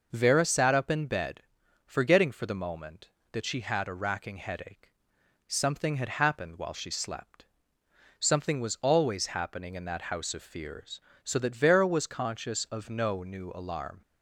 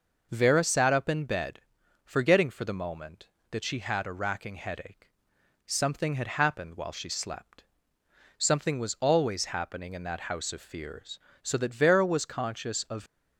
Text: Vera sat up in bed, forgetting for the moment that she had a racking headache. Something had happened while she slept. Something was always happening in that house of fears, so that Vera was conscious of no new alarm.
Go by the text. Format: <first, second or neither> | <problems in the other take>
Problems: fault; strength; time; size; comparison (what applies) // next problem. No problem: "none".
first | stops before "no new alarm"; at 13.0 s